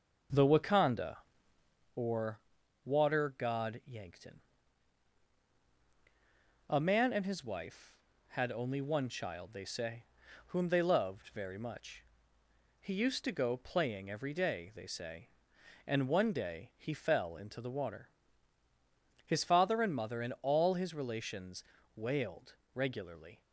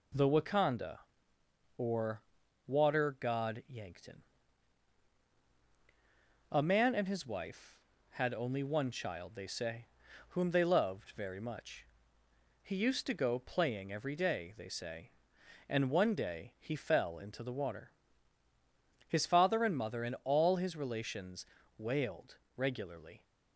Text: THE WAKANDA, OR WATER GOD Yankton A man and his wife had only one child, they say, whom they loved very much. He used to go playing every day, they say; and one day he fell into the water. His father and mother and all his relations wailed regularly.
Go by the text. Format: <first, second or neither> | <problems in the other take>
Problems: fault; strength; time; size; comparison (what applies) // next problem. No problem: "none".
second | starts louder than the rest; noticeable; until 1.9 s; 6 dB // pauses between "OR" and "WATER"; noticeable; at 2.3 s; 0.46 s long; noticeable in the second // pauses between "Yankton" and "A"; strong; at 4.3 s; 2.3 s long; strong in the second // pauses between "relations" and "wailed"; slight; at 21.6 s; 0.36 s long; slight in the second // pauses between "wailed" and "regularly"; slight; at 22.5 s; 0.20 s long; slight in the second